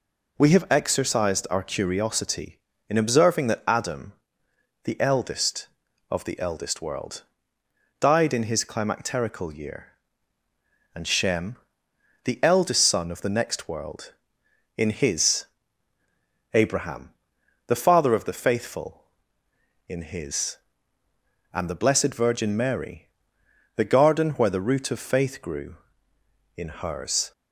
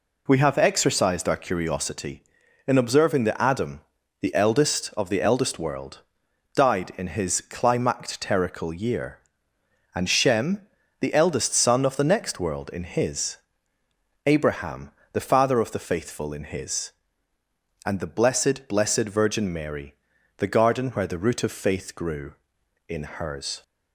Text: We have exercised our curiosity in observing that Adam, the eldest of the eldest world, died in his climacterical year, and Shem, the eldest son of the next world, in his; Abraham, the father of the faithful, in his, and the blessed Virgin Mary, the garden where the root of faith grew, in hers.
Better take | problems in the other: first | says "blessed" twice; at 18.6 s

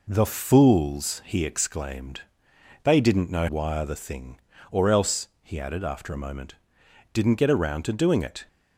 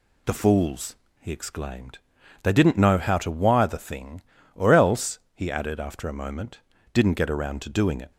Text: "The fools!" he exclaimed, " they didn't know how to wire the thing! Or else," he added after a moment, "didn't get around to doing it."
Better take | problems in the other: second | skips "how to"; at 3.4 s

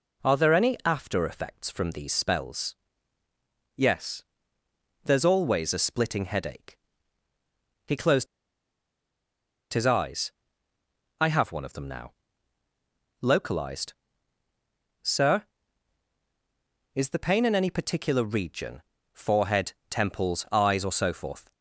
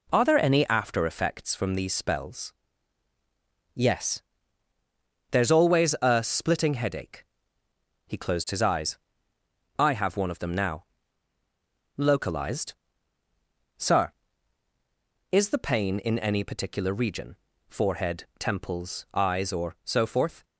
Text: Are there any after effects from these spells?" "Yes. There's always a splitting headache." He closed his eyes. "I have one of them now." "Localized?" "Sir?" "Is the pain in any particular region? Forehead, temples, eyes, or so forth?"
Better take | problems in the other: second | pauses between "closed" and "his"; strong; at 8.2 s; 1.4 s long

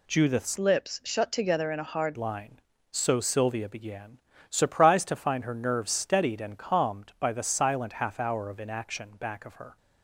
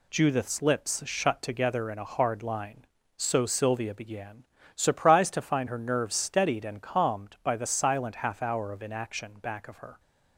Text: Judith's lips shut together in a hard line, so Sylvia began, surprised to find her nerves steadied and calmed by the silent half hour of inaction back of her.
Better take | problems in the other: second | changes voice from "lips" to "hard"; from 0.5 to 2.1 s; 1.6 s long

